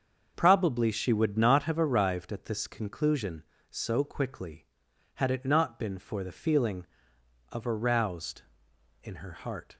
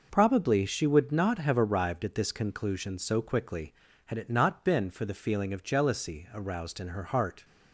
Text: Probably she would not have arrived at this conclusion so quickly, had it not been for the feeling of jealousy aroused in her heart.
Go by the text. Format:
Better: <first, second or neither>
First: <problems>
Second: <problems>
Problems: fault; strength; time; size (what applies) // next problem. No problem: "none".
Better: second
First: starts louder than the rest; until 1.3 s; 6.5 dB // skips "jealousy"; at 7.6 s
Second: none